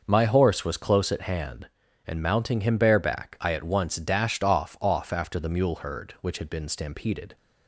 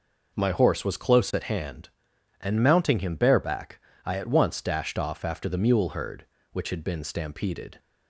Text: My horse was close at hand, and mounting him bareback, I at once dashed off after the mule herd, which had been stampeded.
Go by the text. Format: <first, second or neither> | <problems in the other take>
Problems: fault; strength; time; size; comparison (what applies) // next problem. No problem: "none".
second | starts louder than the rest; noticeable; until 1.0 s; 6 dB // says "off" twice; at 4.8 s